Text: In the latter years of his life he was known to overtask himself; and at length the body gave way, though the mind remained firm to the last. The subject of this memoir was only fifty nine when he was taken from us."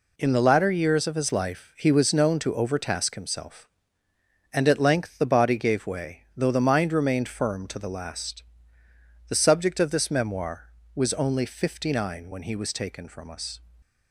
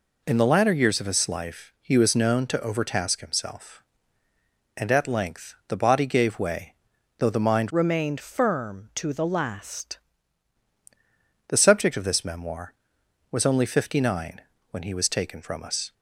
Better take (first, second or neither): first